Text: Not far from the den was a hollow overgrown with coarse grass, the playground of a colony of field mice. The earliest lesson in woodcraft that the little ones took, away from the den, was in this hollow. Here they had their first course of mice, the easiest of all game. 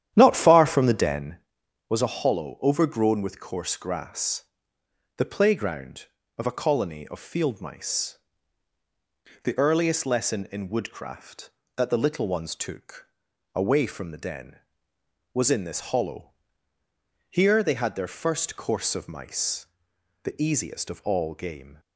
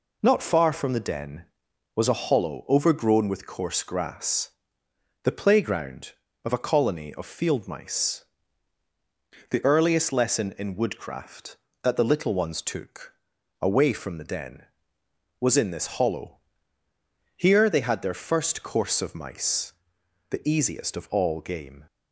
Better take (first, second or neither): second